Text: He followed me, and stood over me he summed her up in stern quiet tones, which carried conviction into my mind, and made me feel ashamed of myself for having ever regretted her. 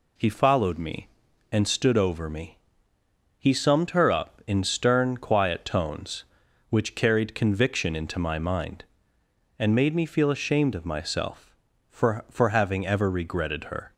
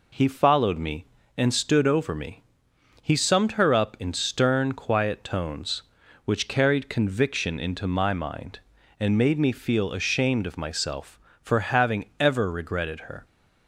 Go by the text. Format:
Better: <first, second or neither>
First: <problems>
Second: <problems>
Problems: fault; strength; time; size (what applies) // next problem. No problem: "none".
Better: second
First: pauses between "me" and "he"; noticeable; at 2.5 s; 0.80 s long // says "for" twice; at 12.2 s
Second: pauses between "me" and "he"; noticeable; at 2.4 s; 0.58 s long